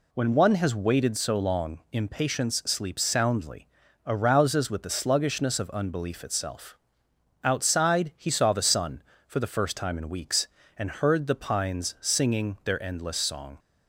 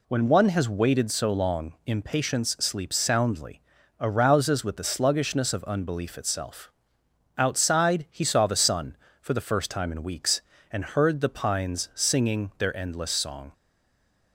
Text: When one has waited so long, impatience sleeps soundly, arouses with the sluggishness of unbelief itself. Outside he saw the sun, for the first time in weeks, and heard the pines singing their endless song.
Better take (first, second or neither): first